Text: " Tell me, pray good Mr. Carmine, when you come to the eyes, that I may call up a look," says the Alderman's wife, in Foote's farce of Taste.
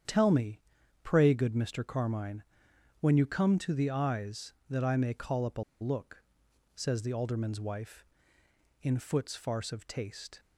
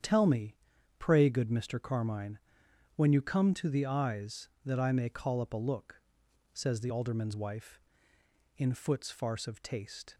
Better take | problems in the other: second | starts louder than the rest; strong; until 1.4 s; 8.5 dB; strong in the second // pauses between "a" and "look"; slight; at 5.6 s; 0.18 s long

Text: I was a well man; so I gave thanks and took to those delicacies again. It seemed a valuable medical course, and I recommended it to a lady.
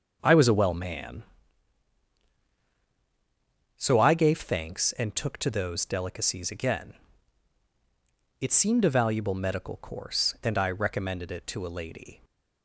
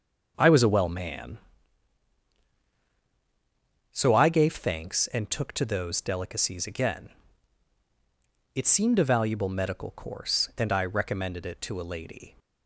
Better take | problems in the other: neither | starts louder than the rest; the same in both

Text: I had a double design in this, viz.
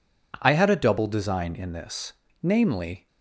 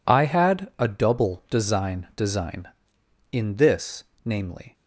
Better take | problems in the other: first | says "design" twice; at 2.1 s

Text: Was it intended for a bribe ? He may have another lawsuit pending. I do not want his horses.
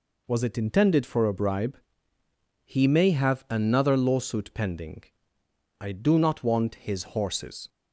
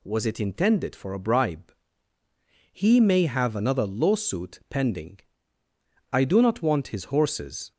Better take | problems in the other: neither | none

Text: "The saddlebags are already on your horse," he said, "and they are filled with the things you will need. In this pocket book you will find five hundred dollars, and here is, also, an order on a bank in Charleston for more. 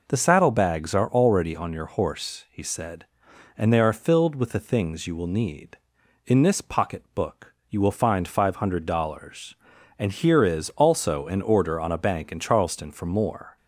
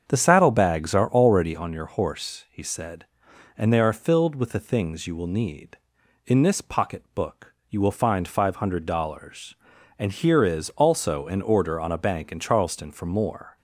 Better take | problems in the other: first | starts louder than the rest; strong; until 1.7 s; 7 dB // pauses between "book" and "you"; slight; at 7.5 s; 0.16 s long; slight in the first

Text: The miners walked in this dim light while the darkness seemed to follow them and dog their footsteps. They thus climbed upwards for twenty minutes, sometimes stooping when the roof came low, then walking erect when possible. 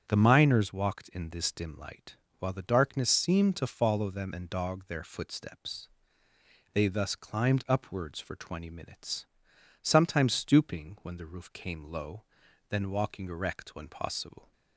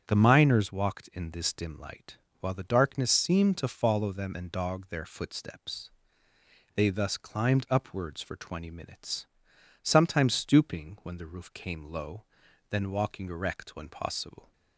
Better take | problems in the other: neither | starts louder than the rest; strong; the same in both // pauses between "light" and "while"; slight; the same in both

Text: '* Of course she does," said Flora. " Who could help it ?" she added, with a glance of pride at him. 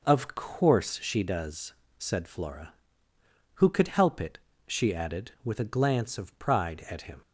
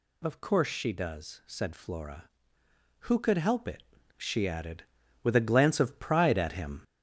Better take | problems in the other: first | gets louder; strong; throughout; 7.5 dB

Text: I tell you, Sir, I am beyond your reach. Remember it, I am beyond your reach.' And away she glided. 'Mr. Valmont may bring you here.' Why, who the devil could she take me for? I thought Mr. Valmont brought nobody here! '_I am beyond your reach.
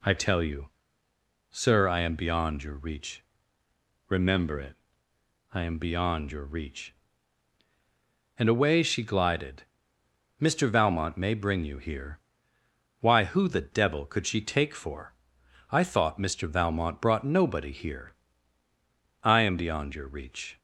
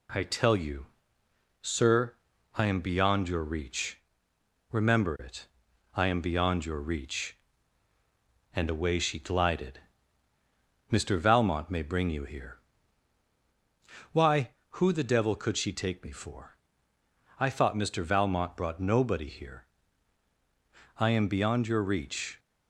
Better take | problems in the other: second | skips "me"; at 14.7 s

